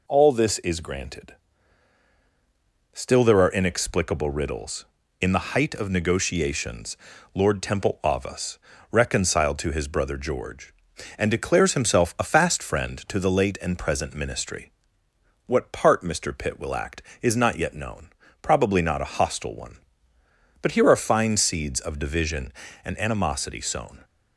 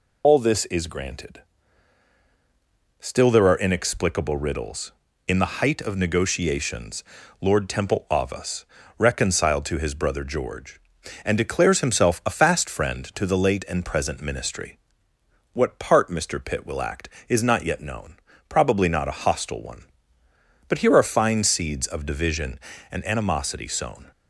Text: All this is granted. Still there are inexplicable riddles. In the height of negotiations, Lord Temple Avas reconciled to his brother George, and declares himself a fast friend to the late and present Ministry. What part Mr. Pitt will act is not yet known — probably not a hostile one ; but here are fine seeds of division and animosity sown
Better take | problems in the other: first | loses the start of "All"; at 0.2 s; 100 ms // pauses between "Avas" and "reconciled"; slight; at 8.6 s; 0.34 s long; slight in the first

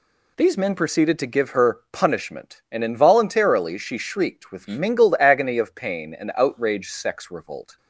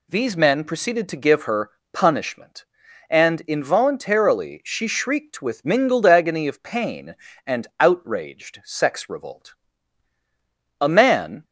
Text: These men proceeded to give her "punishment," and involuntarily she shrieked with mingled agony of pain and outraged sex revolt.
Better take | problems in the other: first | pauses between "her" and "punishment"; slight; at 1.7 s; 0.22 s long // goes on to say "A man"; noticeable; from 10.8 s on; 0.64 s long

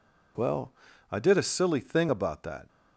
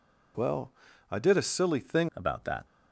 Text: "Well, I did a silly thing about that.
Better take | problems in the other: first | changes voice at "about"; from 2.1 s on; 0.5 s long

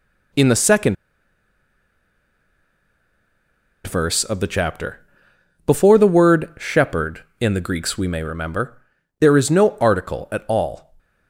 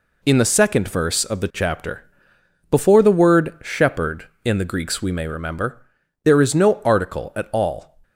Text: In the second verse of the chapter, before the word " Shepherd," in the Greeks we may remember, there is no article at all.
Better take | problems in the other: second | pauses between "second" and "verse"; strong; at 0.9 s; 2.9 s long

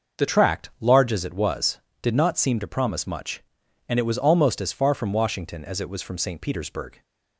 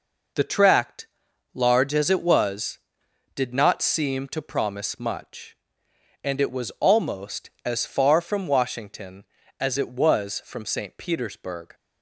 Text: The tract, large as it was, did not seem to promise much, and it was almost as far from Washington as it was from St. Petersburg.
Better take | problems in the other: second | changes voice at "tract"; from 0.2 s on; 6.8 s long

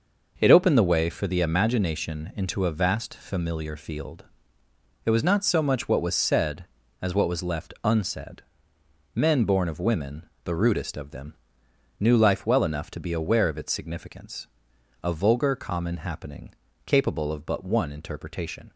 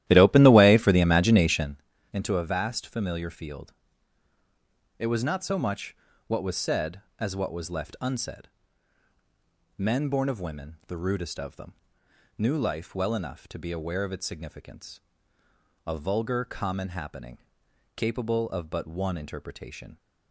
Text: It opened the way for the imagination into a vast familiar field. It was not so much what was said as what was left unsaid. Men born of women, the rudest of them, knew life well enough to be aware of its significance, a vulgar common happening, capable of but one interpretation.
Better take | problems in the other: first | starts louder than the rest; strong; until 1.9 s; 13.5 dB // pauses between "imagination" and "into"; slight; at 1.8 s; 0.32 s long // pauses between "much" and "what"; slight; at 5.9 s; 0.30 s long

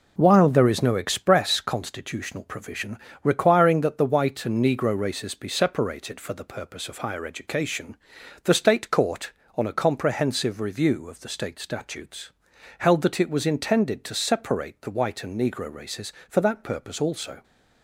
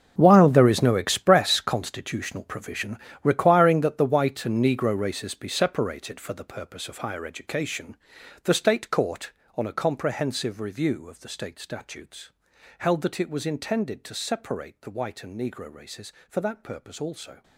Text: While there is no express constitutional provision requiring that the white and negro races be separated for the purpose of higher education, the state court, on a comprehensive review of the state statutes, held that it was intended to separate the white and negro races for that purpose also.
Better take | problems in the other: first | gets quieter; strong; throughout; 14.5 dB // pauses between "provision" and "requiring"; slight; at 2.9 s; 0.26 s long; slight in the first

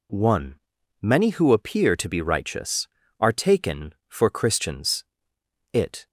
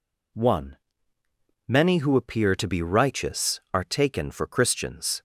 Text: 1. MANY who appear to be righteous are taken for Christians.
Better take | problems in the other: second | goes on to say "It"; slight; from 5.7 s on; 0.36 s long

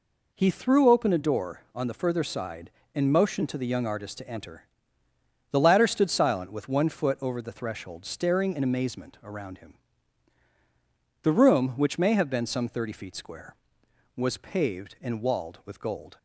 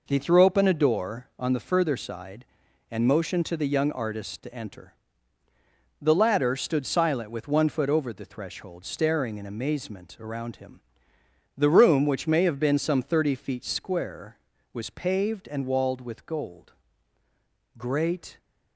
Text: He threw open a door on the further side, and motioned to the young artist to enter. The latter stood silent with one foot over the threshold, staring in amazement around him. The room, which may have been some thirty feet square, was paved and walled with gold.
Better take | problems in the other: first | goes on to say "Great"; noticeable; from 17.7 s on; 0.62 s long

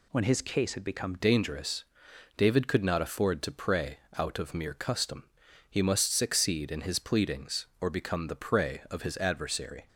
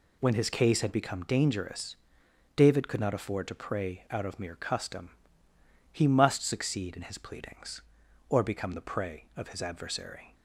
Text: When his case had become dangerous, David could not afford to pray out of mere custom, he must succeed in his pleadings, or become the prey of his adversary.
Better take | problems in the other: second | changes voice at "dangerous"; from 1.1 s on; 8.7 s long // pauses between "pray" and "out"; slight; at 3.9 s; 0.18 s long

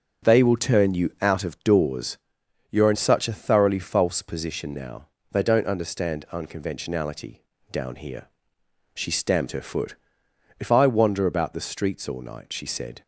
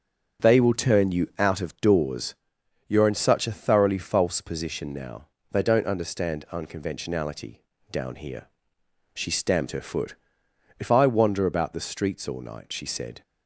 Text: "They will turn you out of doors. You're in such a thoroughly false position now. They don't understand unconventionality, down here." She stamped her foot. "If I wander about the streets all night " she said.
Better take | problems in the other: neither | starts louder than the rest; the same in both

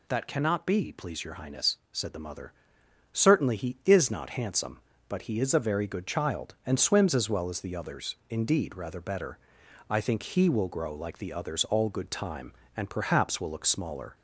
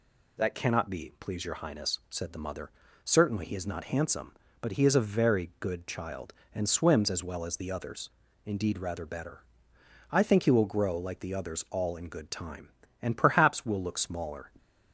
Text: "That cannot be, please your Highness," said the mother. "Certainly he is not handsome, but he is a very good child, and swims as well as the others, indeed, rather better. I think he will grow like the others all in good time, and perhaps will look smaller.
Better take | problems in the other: second | skips "in"; at 11.8 s

